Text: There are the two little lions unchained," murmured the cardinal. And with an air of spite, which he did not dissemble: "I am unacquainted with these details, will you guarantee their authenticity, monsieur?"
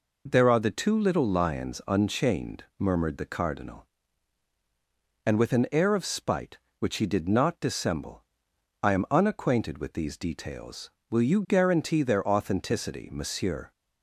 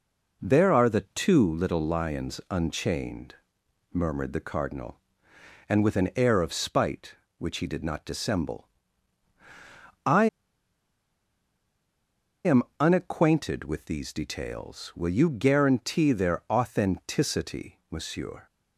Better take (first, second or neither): first